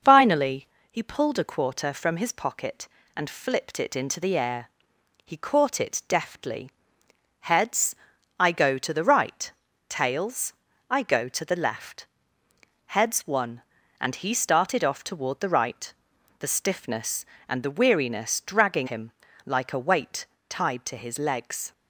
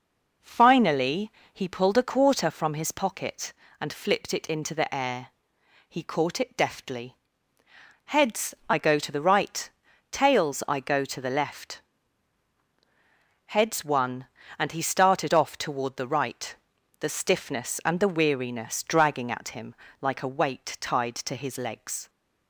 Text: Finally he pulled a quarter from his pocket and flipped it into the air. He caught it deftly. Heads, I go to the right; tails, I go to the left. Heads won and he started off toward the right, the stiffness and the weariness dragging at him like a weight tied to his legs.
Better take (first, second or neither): second